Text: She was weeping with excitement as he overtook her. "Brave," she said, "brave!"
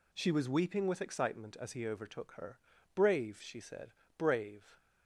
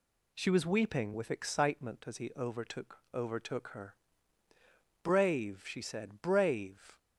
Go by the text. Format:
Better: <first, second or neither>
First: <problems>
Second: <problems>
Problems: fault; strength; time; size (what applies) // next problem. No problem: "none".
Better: first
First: none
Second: says "overtook" twice; at 3.1 s